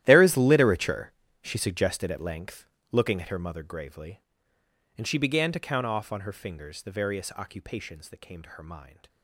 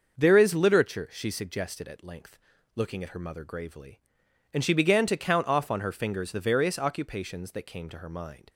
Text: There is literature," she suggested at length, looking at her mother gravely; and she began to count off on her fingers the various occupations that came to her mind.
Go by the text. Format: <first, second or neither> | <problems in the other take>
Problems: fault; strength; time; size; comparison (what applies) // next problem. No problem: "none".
second | gets quieter; strong; throughout; 18 dB // starts louder than the rest; strong; until 1.0 s; 13 dB; noticeable in the second